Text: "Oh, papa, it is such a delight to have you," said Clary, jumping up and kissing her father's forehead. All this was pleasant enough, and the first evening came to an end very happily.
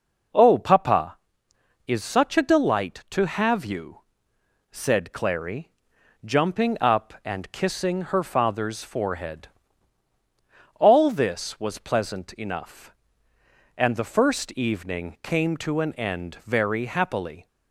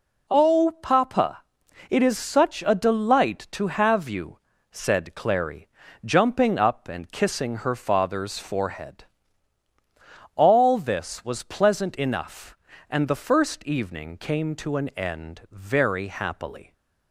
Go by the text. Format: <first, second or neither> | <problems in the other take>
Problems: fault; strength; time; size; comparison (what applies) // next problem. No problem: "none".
second | skips "it"; at 1.5 s